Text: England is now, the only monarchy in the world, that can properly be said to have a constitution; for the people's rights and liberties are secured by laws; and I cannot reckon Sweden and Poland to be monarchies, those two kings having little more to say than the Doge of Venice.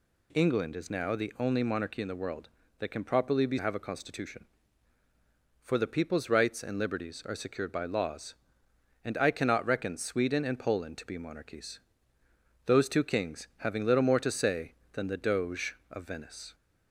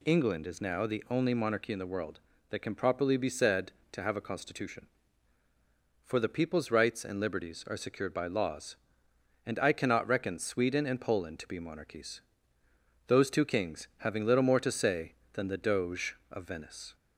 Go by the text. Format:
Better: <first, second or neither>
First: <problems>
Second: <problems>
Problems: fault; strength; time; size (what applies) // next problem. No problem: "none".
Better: second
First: skips "said to"; at 3.5 s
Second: none